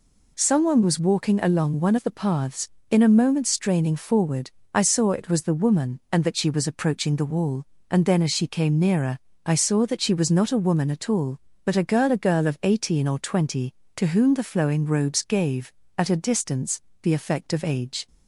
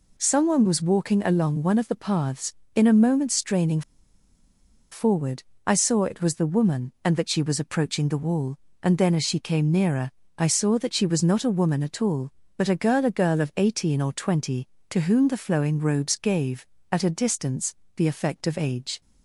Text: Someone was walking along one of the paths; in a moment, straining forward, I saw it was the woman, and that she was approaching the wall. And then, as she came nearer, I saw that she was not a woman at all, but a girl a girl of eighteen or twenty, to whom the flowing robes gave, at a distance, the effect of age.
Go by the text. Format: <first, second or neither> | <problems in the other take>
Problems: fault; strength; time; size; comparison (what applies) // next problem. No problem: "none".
first | pauses between "straining" and "forward"; at 3.8 s; 1.1 s long